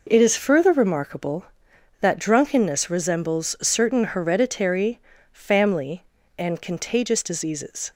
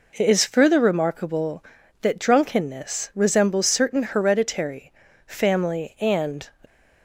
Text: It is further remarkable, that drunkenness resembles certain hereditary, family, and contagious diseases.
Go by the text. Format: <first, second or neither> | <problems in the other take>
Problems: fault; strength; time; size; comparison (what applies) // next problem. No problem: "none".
first | stops before "contagious diseases"; at 6.6 s